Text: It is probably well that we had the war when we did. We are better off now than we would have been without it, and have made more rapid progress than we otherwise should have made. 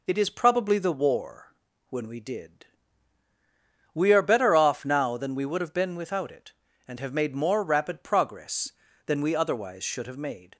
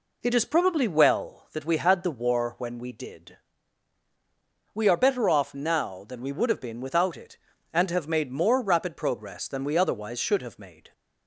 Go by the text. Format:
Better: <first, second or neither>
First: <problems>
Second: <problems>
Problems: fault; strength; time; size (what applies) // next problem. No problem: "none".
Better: second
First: skips "well that we had"; at 0.7 s // pauses between "war" and "when"; slight; at 1.5 s; 0.36 s long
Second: none